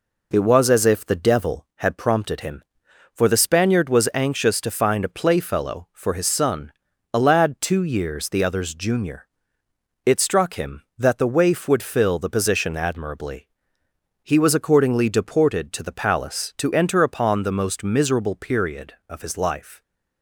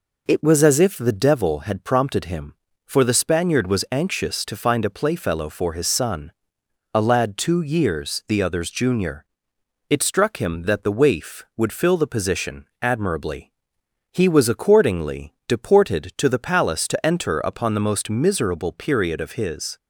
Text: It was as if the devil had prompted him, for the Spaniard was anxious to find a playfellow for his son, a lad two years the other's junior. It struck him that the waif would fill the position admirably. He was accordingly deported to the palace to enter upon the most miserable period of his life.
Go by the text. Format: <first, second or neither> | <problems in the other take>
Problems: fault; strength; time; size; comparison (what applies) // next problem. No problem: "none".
first | pauses between "position" and "admirably"; slight; at 12.6 s; 0.16 s long // stops before "life"; at 19.7 s